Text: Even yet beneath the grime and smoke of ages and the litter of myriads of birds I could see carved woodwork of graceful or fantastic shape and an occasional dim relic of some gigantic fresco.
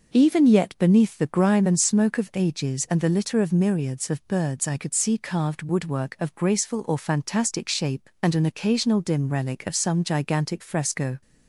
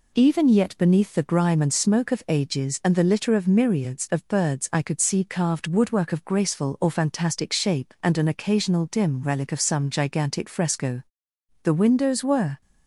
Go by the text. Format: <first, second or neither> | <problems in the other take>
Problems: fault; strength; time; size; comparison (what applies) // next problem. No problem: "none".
first | goes on to say "The windows were"; noticeable; from 11.6 s on; 0.98 s long